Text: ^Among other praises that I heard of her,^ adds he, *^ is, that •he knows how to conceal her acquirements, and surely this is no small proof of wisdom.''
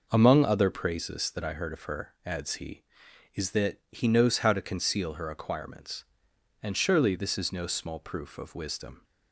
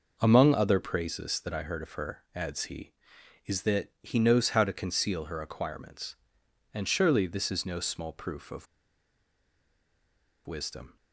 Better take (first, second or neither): first